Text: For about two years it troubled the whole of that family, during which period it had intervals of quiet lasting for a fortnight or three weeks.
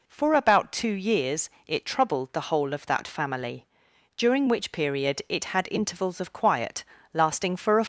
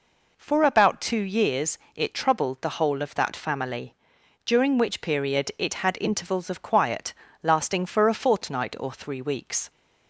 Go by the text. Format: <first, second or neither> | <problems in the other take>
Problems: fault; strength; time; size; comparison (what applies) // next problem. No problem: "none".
second | pauses between "years" and "it"; slight; at 1.4 s; 0.16 s long; slight in the second // pauses between "quiet" and "lasting"; slight; at 6.8 s; 0.30 s long; slight in the second // stops before "fortnight or three weeks"; at 7.8 s